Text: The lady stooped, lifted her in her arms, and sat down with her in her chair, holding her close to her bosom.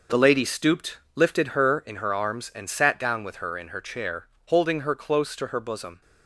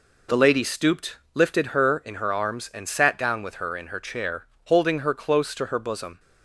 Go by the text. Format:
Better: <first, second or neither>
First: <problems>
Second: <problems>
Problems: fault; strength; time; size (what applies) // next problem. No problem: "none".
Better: second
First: gets quieter; strong; throughout; 8.5 dB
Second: none